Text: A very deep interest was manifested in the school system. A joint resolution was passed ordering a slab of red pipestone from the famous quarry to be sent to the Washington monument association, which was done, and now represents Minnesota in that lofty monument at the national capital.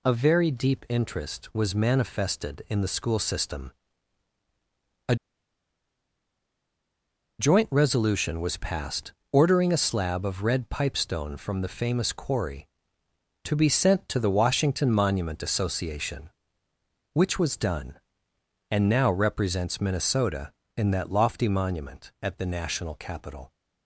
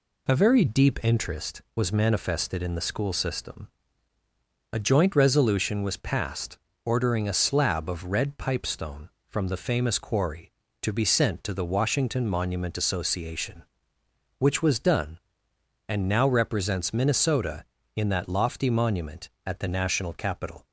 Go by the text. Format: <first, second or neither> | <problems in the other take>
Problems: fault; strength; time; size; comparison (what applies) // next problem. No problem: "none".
second | pauses between "A" and "joint"; strong; at 5.1 s; 2.2 s long // pauses between "passed" and "ordering"; slight; at 9.1 s; 0.18 s long; slight in the second